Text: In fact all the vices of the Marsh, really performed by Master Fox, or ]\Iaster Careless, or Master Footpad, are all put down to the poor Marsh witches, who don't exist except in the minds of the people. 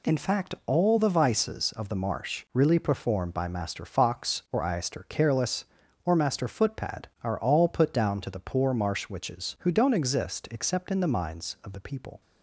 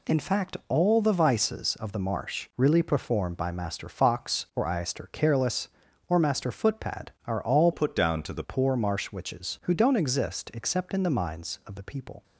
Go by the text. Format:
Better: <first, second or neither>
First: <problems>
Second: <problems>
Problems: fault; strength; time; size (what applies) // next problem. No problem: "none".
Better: first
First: none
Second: changes voice from "put" to "the"; from 7.7 to 8.4 s; 0.7 s long